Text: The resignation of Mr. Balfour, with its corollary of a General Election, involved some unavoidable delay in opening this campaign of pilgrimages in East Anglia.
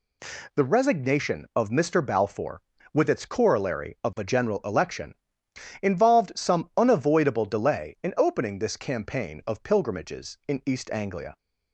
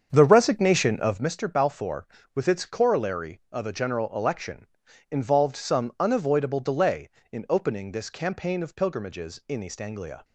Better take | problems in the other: first | starts louder than the rest; strong; until 1.4 s; 7.5 dB

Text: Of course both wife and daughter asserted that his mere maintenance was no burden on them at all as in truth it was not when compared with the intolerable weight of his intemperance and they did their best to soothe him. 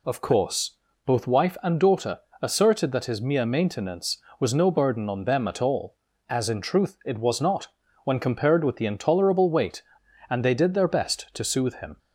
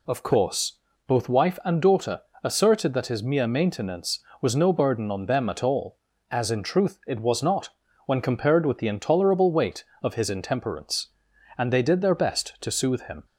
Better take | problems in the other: second | pauses between "course" and "both"; slight; at 0.7 s; 0.30 s long; slight in the second // pauses between "daughter" and "asserted"; slight; at 2.1 s; 0.22 s long; slight in the second // pauses between "not" and "when"; slight; at 7.6 s; 0.36 s long; slight in the second // skips "of his intemperance"; at 10.0 s

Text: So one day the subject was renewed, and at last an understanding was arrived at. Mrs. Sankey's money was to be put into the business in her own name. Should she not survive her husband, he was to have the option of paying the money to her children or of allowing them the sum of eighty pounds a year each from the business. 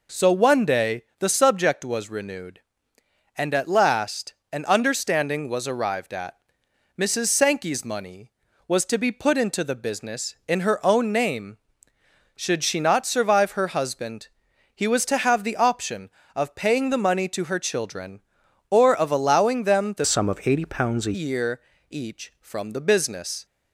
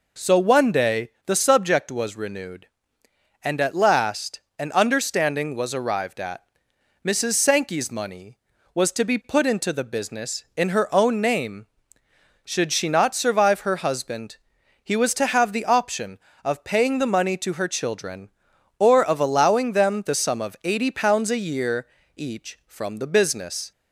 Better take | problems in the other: second | pauses between "day" and "the"; slight; at 1.0 s; 0.16 s long; slight in the second // pauses between "last" and "an"; slight; at 4.3 s; 0.16 s long; slight in the second // changes voice from "sum" to "a"; from 20.0 to 21.1 s; 1.1 s long // pauses between "year" and "each"; slight; at 21.6 s; 0.30 s long; slight in the second

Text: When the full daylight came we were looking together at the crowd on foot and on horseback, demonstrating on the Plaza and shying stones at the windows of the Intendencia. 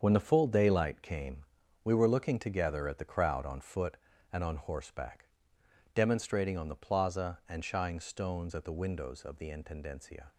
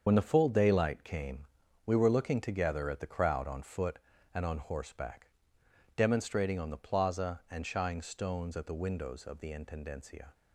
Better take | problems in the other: first | loses the start of "When"; at 0.0 s; 45 ms // starts louder than the rest; until 1.0 s; 7 dB; also in the first // pauses between "came" and "we"; at 1.4 s; 0.40 s long; also in the first

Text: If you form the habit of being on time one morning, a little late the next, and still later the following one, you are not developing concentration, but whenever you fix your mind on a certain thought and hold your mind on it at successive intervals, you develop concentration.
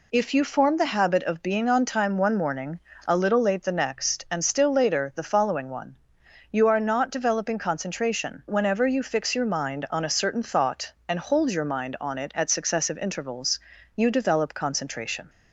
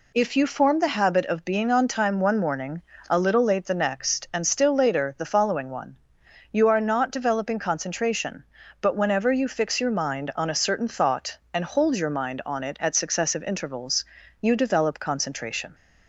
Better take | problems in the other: second | skips "but"; at 8.4 s

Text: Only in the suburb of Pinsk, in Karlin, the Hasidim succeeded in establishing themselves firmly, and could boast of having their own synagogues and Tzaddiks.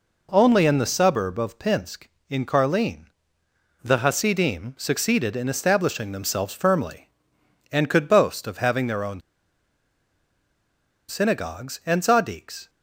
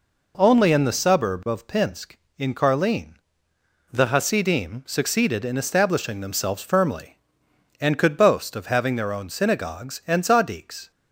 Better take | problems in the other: second | pauses between "own" and "synagogues"; strong; at 9.2 s; 1.8 s long

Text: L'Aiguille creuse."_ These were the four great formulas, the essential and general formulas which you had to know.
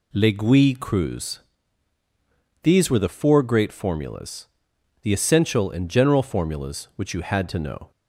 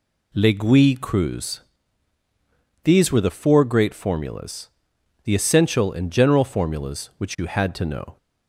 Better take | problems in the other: neither | none

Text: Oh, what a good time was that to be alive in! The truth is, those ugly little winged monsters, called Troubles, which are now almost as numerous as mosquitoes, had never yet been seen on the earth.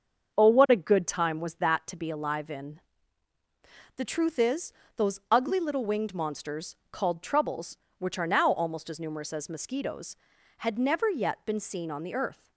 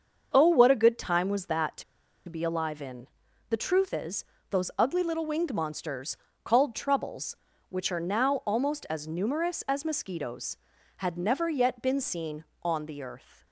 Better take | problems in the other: first | starts louder than the rest; until 1.3 s; 6.5 dB; also in the first // pauses between "to" and "be"; at 1.8 s; 0.45 s long

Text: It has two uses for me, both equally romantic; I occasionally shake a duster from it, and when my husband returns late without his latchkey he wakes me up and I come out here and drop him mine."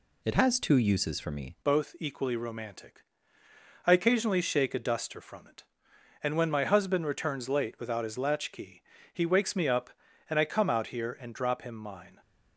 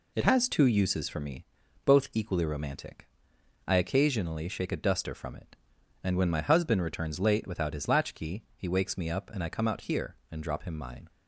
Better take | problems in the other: second | changes voice at "both"; from 1.6 s on; 10.5 s long // pauses between "latchkey" and "he"; slight; at 8.8 s; 0.28 s long

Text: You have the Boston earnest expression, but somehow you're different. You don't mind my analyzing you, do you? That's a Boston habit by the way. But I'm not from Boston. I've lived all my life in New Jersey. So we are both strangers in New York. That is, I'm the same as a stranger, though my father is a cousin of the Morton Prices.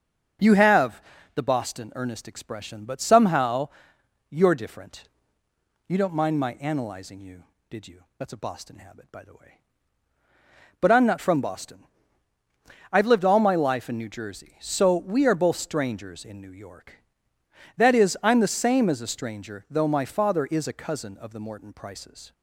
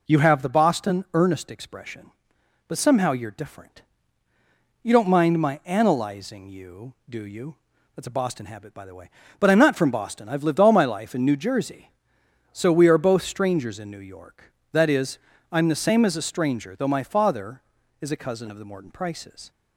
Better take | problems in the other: second | starts louder than the rest; strong; until 1.7 s; 7 dB // pauses between "have" and "the"; slight; at 1.0 s; 0.32 s long // pauses between "somehow" and "you're"; noticeable; at 3.6 s; 0.62 s long // says "did" for "do"; at 7.6 s

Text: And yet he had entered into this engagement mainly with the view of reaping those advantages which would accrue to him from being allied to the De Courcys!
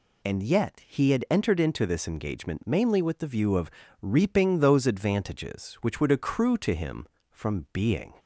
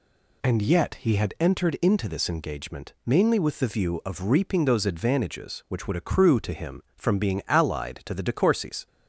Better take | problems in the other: second | pauses between "of" and "reaping"; slight; at 3.6 s; 0.32 s long // stops before "allied to the De Courcys"; at 8.1 s

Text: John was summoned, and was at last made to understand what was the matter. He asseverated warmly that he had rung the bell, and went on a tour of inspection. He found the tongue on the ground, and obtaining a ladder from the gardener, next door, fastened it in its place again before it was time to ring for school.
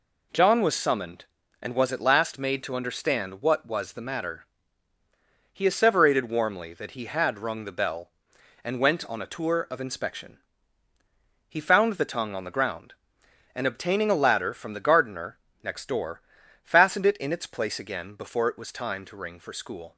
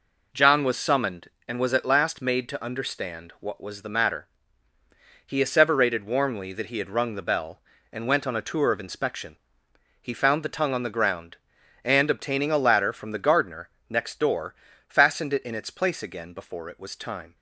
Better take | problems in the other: first | stops before "to ring for school"; at 17.3 s

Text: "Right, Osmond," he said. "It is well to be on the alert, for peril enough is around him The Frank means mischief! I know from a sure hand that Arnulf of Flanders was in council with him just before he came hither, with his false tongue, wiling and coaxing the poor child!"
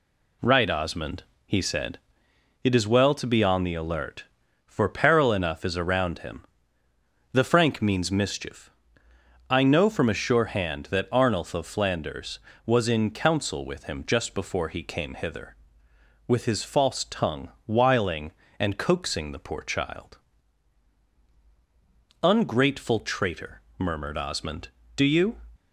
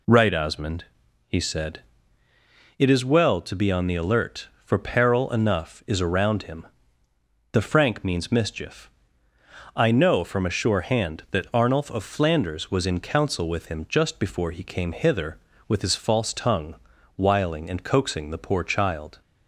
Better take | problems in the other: second | pauses between "him" and "The"; noticeable; at 6.4 s; 0.88 s long; noticeable in the second // goes on to say "Ungrateful traitor murmured Osmond Do you"; strong; from 22.2 s on; 3.1 s long

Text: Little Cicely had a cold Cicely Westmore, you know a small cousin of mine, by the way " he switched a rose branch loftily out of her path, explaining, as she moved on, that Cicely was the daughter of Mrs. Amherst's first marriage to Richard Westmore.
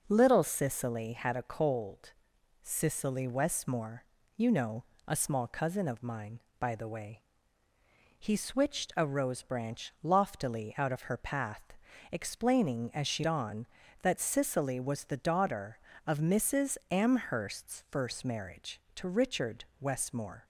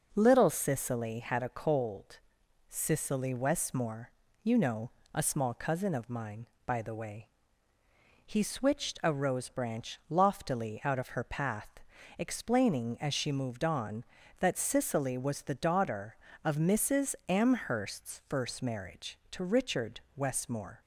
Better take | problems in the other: second | starts louder than the rest; strong; until 1.1 s; 7.5 dB; strong in the second // pauses between "cold" and "Cicely"; noticeable; at 2.1 s; 0.50 s long; noticeable in the second // pauses between "know" and "a"; slight; at 4.8 s; 0.24 s long; slight in the second // skips "moved"; at 13.2 s

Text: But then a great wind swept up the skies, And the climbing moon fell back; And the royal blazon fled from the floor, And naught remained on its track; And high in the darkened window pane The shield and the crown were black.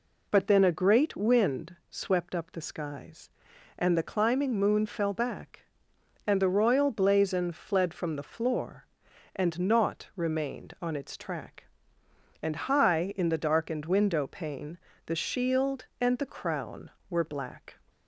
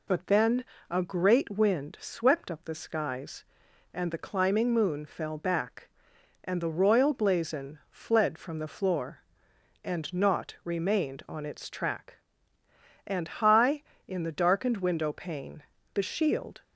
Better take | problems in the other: first | pauses between "then" and "a"; slight; at 0.6 s; 0.24 s long // pauses between "pane" and "The"; slight; at 15.6 s; 0.32 s long; slight in the first // stops before "and the crown were black"; at 16.6 s

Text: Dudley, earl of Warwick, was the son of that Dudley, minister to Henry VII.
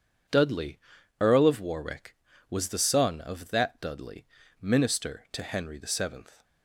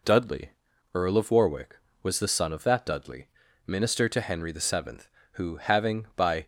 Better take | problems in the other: first | goes on to say "who having by"; noticeable; from 5.3 s on; 1.0 s long

